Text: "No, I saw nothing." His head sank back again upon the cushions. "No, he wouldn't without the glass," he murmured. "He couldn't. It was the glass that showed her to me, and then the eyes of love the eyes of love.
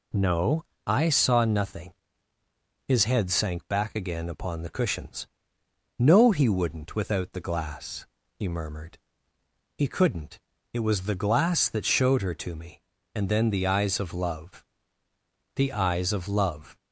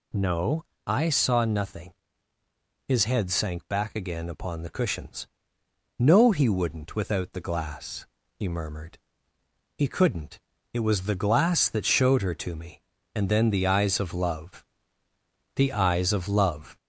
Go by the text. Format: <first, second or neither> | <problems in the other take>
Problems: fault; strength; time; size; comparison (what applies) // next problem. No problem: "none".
first | gets louder; slight; throughout; 2.5 dB // pauses between "love" and "the"; noticeable; at 14.6 s; 0.90 s long; noticeable in the first